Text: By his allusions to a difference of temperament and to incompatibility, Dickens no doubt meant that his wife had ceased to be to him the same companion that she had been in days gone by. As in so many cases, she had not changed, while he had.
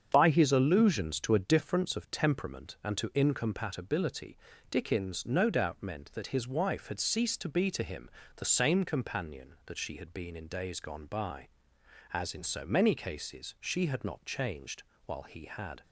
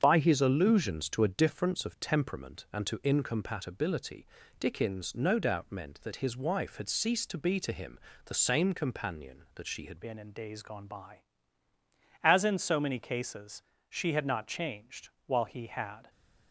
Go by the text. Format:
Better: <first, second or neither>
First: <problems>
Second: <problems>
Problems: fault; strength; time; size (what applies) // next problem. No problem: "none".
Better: first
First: starts louder than the rest; strong; until 1.1 s; 7.5 dB // pauses between "him" and "the"; slight; at 8.1 s; 0.24 s long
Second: starts louder than the rest; strong; until 1.0 s; 7.5 dB // pauses between "him" and "the"; slight; at 7.9 s; 0.24 s long // changes voice at "been"; from 10.0 s on; 6.0 s long